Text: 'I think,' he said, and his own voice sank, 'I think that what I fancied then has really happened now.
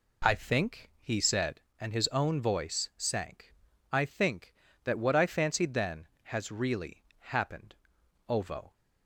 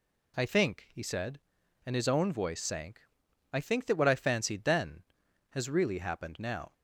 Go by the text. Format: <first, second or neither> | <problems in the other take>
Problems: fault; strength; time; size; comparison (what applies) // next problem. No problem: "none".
second | pauses between "really" and "happened"; slight; at 7.0 s; 0.16 s long // says "ovo" for "now"; at 8.2 s